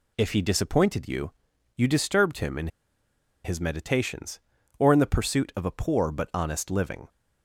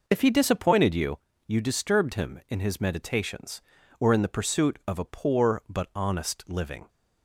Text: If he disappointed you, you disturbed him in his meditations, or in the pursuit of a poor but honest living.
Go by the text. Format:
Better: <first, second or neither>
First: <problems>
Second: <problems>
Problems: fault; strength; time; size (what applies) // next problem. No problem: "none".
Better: second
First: pauses between "in" and "his"; noticeable; at 2.6 s; 0.76 s long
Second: none